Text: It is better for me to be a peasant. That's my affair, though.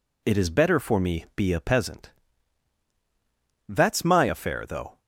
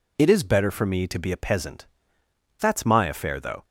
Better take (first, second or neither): second